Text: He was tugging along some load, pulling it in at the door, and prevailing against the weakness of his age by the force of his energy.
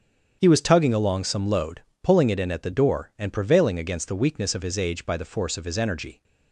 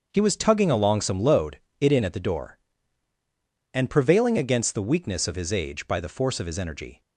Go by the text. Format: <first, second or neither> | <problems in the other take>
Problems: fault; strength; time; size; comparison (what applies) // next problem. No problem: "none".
first | starts louder than the rest; until 1.1 s; 6.5 dB; strong in the first // skips "pulling"; at 1.6 s